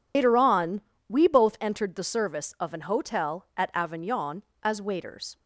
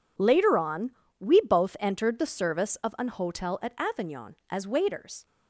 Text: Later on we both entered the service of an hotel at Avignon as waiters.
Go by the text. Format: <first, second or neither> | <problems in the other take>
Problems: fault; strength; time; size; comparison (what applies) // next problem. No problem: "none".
second | loses the start of "Later"; at 0.1 s; 125 ms // pauses between "on" and "we"; slight; at 0.8 s; 0.26 s long; slight in the second